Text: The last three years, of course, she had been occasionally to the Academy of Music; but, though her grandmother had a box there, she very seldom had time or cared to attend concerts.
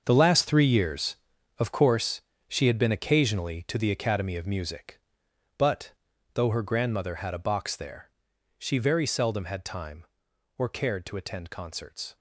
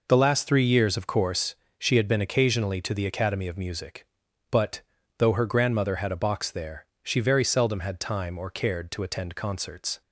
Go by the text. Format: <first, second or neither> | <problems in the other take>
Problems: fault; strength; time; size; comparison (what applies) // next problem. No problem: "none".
second | gets quieter; strong; throughout; 13 dB